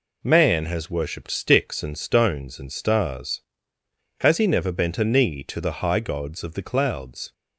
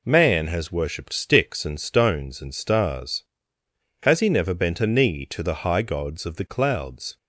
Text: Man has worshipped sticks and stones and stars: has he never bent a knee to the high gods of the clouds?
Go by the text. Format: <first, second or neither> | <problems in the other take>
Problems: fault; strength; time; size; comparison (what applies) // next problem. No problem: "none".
neither | none